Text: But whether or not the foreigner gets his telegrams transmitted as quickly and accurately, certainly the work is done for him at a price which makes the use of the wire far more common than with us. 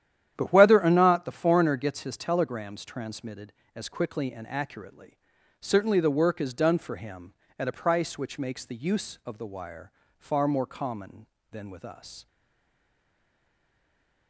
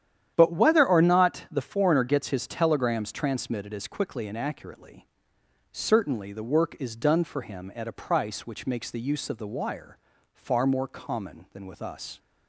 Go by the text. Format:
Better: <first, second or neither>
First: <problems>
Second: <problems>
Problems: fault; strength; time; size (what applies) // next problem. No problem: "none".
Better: second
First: starts louder than the rest; strong; until 1.3 s; 10.5 dB // pauses between "wire" and "far"; slight; at 9.9 s; 0.28 s long // stays silent after the last word; noticeable; from 12.2 s on; 2.0 s long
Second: starts louder than the rest; strong; until 1.3 s; 10 dB // pauses between "wire" and "far"; at 9.9 s; 0.38 s long